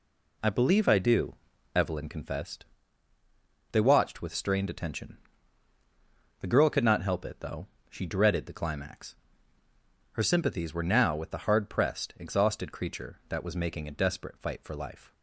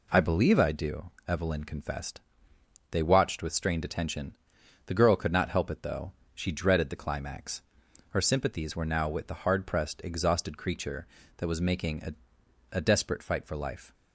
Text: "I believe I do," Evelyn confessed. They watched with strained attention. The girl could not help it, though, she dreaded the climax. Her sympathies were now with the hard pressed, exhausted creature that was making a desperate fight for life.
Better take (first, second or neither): first